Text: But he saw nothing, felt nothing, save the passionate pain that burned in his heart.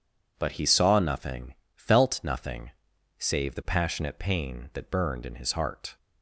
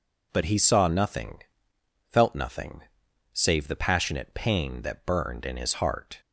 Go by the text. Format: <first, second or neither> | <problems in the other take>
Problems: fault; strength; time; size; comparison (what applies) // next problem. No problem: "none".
neither | none